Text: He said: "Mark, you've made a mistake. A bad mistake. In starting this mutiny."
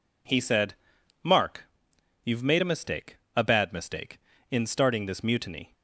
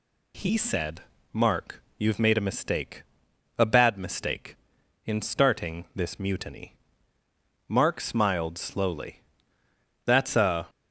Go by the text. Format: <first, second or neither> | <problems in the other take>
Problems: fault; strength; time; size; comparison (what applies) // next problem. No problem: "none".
first | goes on to say "Mark smiled slowly That's a"; strong; from 7.6 s on; 3.0 s long